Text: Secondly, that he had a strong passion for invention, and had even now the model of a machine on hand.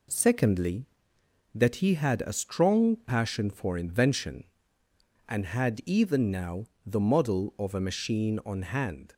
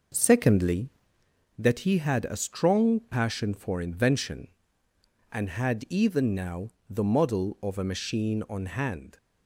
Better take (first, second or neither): first